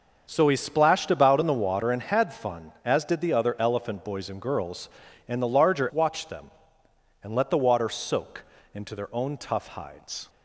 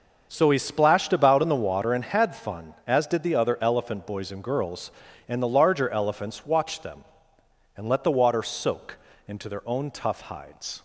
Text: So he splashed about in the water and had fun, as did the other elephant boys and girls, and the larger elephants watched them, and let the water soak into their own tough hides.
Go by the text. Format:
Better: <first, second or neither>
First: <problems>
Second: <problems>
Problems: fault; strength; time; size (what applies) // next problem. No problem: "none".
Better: second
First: starts louder than the rest; until 1.3 s; 6.5 dB // skips "elephants"; at 5.8 s // pauses between "soak" and "into"; slight; at 8.4 s; 0.28 s long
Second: starts louder than the rest; until 1.3 s; 6.5 dB // pauses between "soak" and "into"; slight; at 8.9 s; 0.28 s long